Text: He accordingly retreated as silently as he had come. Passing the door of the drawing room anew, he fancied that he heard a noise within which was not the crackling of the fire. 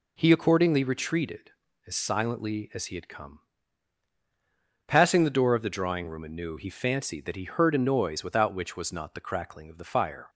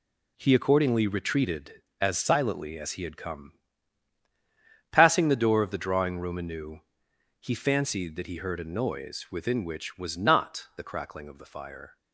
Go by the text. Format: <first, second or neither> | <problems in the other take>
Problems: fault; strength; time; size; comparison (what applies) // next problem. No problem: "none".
second | says "without" for "within"; at 8.2 s